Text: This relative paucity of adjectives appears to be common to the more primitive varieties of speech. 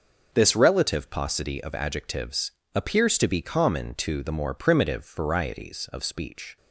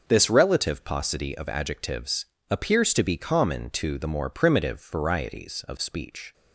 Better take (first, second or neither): neither